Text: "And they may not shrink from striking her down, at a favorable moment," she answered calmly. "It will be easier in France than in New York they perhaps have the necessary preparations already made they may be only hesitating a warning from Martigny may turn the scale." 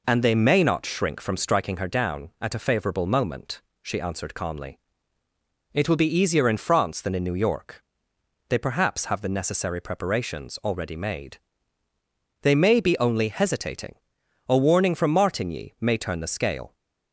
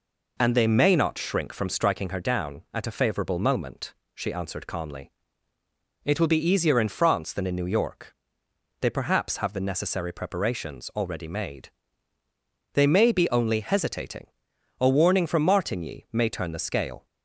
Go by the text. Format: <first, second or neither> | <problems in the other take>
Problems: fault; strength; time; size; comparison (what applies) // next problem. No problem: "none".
neither | pauses between "York" and "they"; noticeable; the same in both // pauses between "made" and "they"; the same in both // pauses between "hesitating" and "a"; noticeable; the same in both